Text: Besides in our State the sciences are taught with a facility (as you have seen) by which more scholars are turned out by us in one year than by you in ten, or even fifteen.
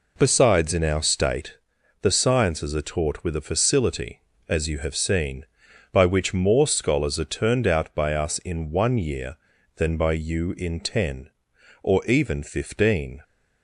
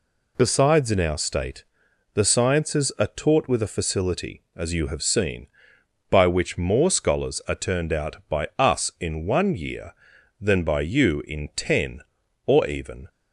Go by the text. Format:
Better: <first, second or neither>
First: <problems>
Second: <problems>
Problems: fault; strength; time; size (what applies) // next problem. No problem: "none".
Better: first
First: pauses between "State" and "the"; at 1.5 s; 0.44 s long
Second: pauses between "State" and "the"; noticeable; at 1.6 s; 0.50 s long // stops before "fifteen"; at 13.0 s